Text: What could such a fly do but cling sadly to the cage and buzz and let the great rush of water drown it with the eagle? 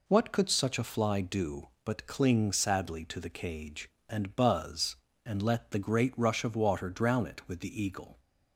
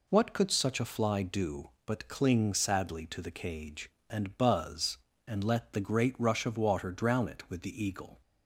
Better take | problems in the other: neither | none

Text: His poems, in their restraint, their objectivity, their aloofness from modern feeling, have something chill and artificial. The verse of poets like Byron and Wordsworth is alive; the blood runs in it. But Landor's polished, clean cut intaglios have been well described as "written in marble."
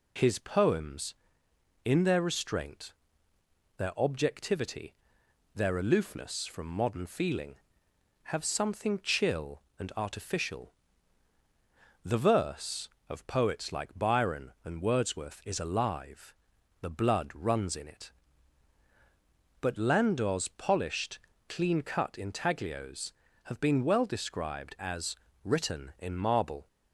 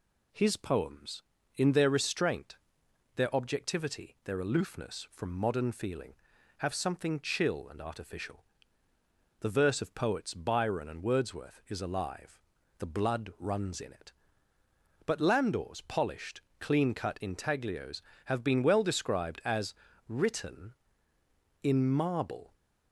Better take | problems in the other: first | skips "like"; at 10.3 s // pauses between "as" and "written"; slight; at 19.7 s; 0.34 s long; slight in the first

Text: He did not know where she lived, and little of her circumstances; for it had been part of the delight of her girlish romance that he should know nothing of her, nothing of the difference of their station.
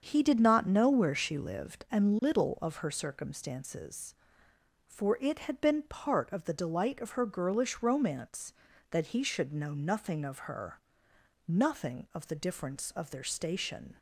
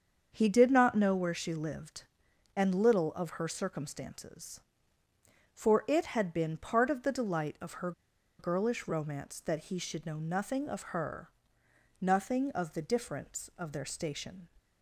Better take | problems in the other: first | starts louder than the rest; until 1.3 s; 7 dB; also in the first // pauses between "her" and "girlish"; noticeable; at 7.9 s; 0.48 s long

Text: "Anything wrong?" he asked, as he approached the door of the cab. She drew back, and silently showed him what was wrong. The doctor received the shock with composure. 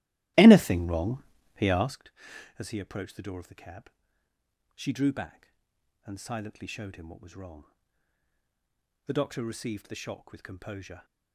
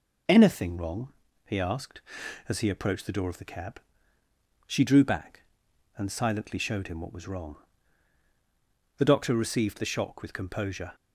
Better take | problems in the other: second | starts louder than the rest; strong; until 2.1 s; 15.5 dB

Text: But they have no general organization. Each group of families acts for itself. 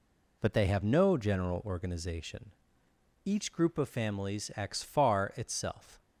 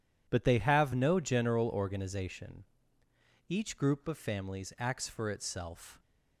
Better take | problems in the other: second | says "far" for "for"; at 4.8 s

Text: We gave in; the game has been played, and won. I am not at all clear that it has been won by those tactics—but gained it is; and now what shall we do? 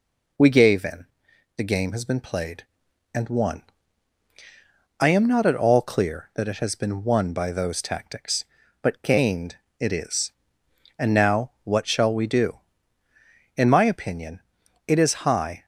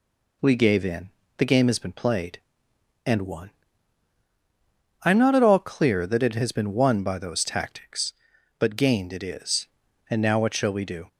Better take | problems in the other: second | pauses between "gained" and "it"; slight; at 9.5 s; 0.22 s long // goes on to say "In my opinion it is high"; strong; from 13.5 s on; 2.0 s long

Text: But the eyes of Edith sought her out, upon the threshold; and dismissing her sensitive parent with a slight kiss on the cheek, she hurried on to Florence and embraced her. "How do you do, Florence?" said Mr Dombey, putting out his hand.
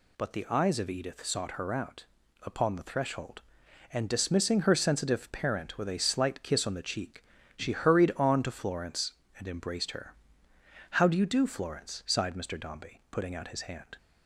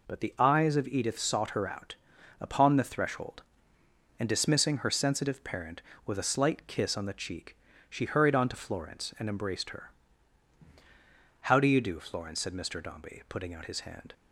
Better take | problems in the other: second | says "sighed" for "said"; at 12.0 s

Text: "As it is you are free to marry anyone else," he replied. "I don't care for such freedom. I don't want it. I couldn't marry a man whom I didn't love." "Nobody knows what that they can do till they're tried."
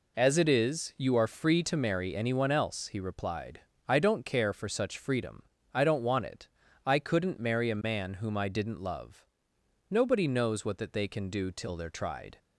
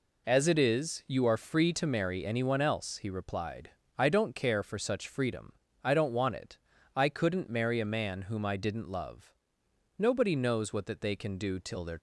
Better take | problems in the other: first | stops before "tried"; at 11.9 s

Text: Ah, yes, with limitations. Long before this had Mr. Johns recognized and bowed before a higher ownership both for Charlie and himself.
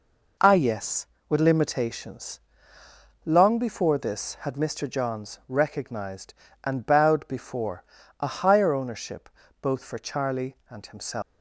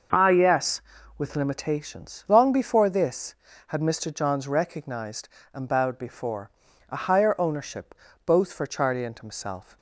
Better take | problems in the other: second | pauses between "before" and "a"; slight; at 7.8 s; 0.36 s long; also in the second // pauses between "ownership" and "both"; slight; at 9.2 s; 0.32 s long; slight in the second // leaves "himself" unfinished; at 11.2 s; 250 ms

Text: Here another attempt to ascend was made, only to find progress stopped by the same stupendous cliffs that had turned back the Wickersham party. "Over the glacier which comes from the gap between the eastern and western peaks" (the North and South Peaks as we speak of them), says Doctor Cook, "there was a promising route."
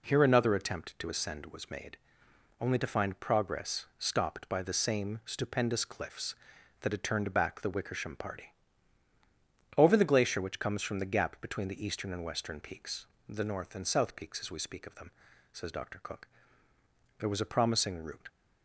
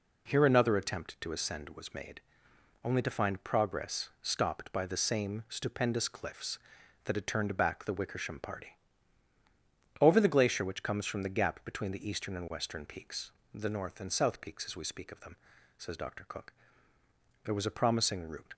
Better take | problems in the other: neither | none

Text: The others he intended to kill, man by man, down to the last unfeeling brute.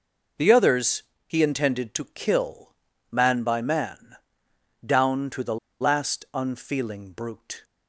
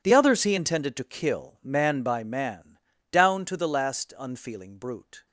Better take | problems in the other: second | pauses between "others" and "he"; slight; at 1.0 s; 0.24 s long // pauses between "the" and "last"; slight; at 5.5 s; 0.24 s long

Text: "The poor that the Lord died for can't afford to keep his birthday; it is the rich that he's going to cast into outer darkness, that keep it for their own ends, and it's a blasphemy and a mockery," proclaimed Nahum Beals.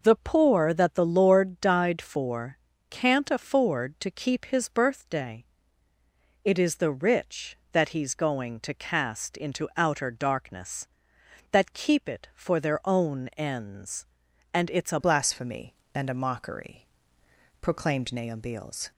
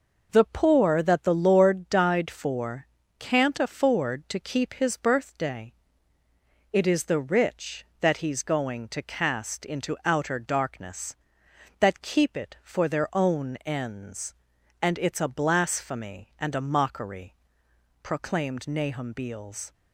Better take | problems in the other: second | pauses between "for" and "can't"; slight; at 2.5 s; 0.32 s long; slight in the second // changes voice at "blasphemy"; from 15.0 s on; 3.9 s long

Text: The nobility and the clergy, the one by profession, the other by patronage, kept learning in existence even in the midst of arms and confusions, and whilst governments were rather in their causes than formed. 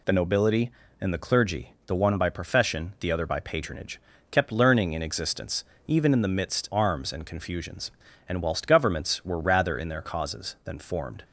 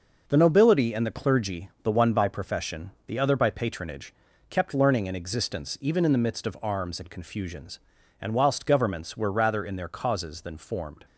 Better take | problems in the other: second | pauses between "existence" and "even"; slight; at 5.6 s; 0.22 s long // skips "of"; at 6.6 s

